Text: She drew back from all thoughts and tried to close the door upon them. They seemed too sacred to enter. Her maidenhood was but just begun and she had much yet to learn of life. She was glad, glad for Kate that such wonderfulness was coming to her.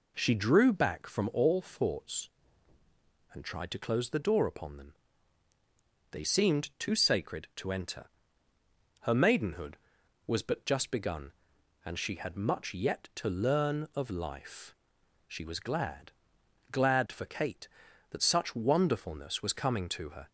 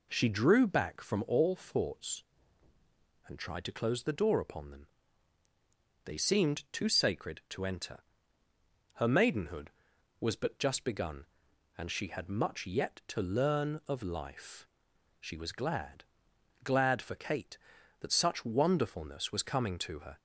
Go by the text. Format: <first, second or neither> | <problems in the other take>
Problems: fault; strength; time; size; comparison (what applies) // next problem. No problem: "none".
neither | none